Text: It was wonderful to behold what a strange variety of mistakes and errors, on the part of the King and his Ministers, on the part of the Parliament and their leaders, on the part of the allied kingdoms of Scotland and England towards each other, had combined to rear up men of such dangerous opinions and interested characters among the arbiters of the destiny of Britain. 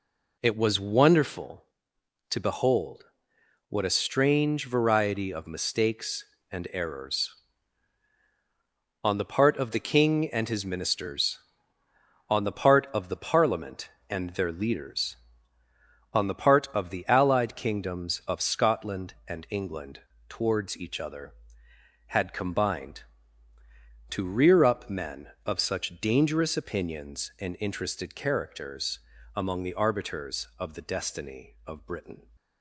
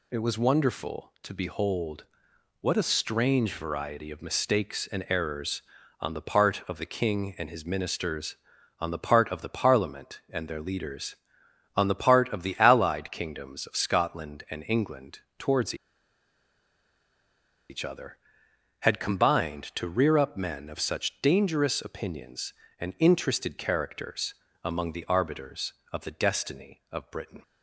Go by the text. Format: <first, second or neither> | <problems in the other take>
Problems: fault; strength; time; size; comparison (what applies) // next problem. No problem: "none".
first | pauses between "behold" and "what"; noticeable; at 2.0 s; 0.56 s long; noticeable in the first // pauses between "England" and "towards"; slight; at 15.1 s; 0.18 s long; slight in the first // pauses between "towards" and "each"; strong; at 15.7 s; 1.9 s long // pauses between "characters" and "among"; slight; at 24.3 s; 0.30 s long; slight in the first